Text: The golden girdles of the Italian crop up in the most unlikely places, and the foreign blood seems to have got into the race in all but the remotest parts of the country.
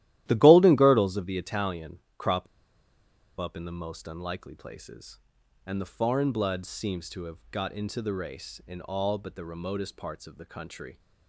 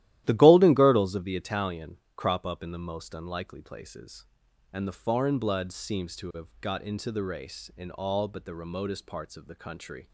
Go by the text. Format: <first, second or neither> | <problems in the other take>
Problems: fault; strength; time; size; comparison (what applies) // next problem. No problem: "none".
second | starts louder than the rest; strong; until 1.2 s; 14 dB; strong in the second // pauses between "Italian" and "crop"; slight; at 1.9 s; 0.18 s long; slight in the second // pauses between "crop" and "up"; noticeable; at 2.4 s; 0.94 s long